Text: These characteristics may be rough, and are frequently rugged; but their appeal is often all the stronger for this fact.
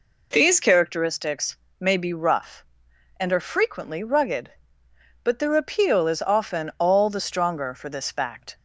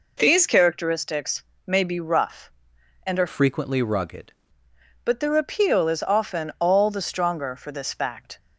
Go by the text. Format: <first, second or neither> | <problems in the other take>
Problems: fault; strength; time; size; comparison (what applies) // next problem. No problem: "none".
first | pauses between "characteristics" and "may"; slight; at 1.4 s; 0.20 s long; slight in the first // changes voice from "frequently" to "rugged"; from 3.2 to 4.3 s; 1.1 s long